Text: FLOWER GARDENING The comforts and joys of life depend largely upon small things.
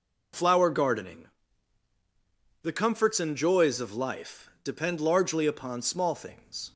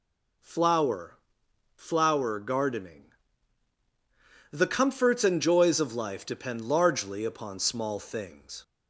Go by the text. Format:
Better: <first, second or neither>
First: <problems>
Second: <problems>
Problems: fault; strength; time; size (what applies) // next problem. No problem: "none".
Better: first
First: pauses between "GARDENING" and "The"; strong; at 1.2 s; 1.3 s long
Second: says "FLOWER" twice; at 1.7 s // pauses between "GARDENING" and "The"; strong; at 3.0 s; 1.4 s long